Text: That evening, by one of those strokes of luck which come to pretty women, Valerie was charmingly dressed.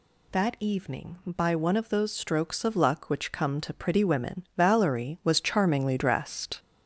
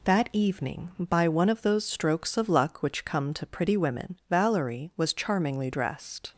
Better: second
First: gets louder; noticeable; throughout; 5.5 dB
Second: none

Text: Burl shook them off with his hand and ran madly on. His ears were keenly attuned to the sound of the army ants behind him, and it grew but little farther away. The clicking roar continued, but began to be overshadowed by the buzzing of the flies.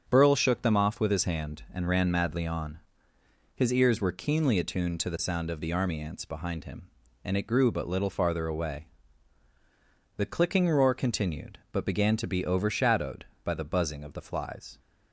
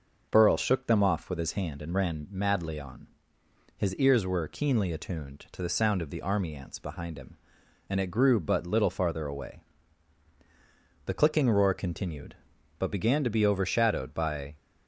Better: first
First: starts louder than the rest; strong; until 1.1 s; 7 dB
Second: starts louder than the rest; noticeable; until 1.3 s; 6 dB // stops before "the buzzing of the flies"; at 14.5 s

